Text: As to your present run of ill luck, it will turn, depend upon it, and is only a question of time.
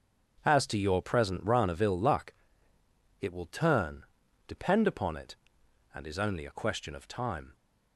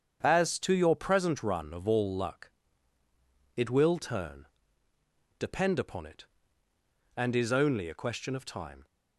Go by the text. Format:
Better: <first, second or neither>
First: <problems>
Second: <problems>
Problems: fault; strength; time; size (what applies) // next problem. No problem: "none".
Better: first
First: starts louder than the rest; strong; until 1.4 s; 7 dB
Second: starts louder than the rest; strong; until 1.2 s; 7.5 dB // says "all" for "ill"; at 1.8 s